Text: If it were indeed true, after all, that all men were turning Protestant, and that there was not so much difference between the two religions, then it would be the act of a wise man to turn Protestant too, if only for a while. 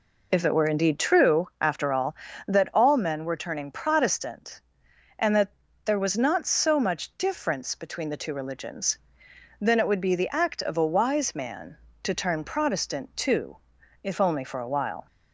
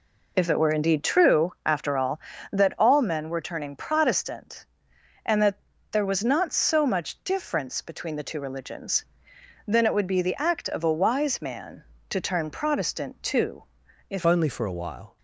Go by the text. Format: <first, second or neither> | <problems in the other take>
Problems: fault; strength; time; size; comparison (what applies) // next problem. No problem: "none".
first | pauses between "that" and "there"; slight; at 5.5 s; 0.36 s long; slight in the first // changes voice at "only"; from 14.2 s on; 0.9 s long